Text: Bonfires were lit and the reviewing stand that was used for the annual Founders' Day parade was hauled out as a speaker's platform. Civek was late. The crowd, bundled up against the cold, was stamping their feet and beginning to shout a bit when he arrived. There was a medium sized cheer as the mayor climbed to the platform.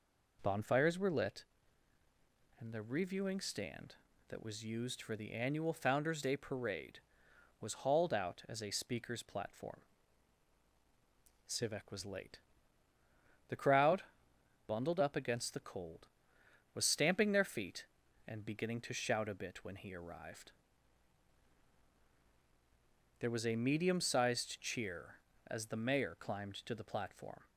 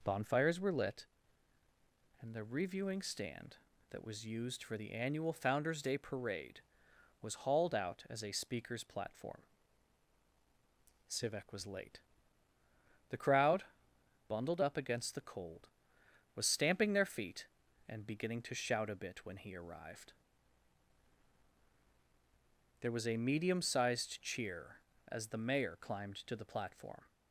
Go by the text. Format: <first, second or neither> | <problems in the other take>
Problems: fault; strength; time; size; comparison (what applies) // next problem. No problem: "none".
neither | none